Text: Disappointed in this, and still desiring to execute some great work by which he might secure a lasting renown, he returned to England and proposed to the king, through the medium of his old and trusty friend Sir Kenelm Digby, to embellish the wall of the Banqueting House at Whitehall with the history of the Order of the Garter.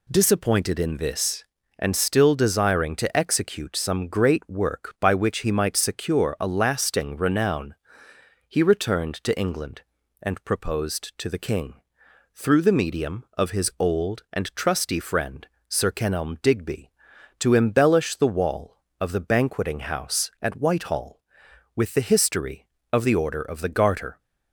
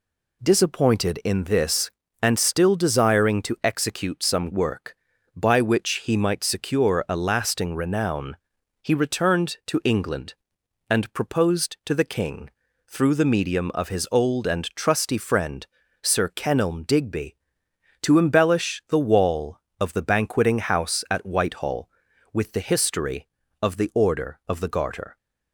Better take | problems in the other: first | skips "great"; at 4.5 s // pauses between "friend" and "Sir"; slight; at 15.6 s; 0.36 s long; slight in the first

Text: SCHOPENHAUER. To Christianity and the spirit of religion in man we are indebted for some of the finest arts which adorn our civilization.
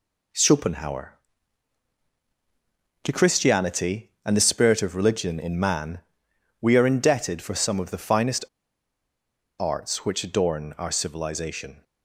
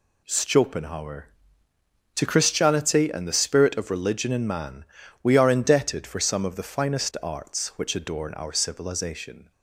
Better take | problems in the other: second | pauses between "man" and "we"; noticeable; at 5.9 s; 0.62 s long; slight in the second // pauses between "finest" and "arts"; at 8.4 s; 1.1 s long

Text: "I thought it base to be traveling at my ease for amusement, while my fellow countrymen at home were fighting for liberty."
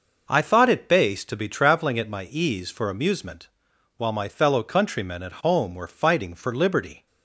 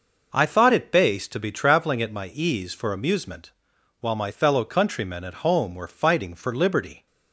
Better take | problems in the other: neither | none

